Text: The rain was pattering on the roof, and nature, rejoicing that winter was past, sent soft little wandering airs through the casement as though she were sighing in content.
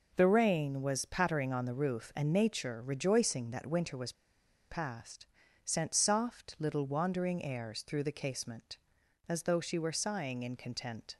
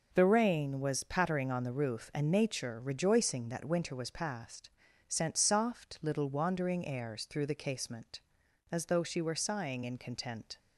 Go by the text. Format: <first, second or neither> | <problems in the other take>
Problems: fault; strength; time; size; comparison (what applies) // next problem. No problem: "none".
second | pauses between "was" and "past"; noticeable; at 4.1 s; 0.57 s long